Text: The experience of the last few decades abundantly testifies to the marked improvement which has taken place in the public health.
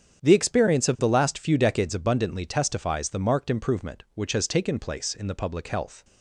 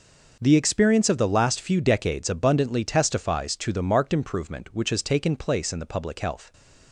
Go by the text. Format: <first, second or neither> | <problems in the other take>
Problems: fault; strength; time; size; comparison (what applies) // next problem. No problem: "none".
second | starts louder than the rest; strong; until 1.2 s; 8 dB // skips "to"; at 3.0 s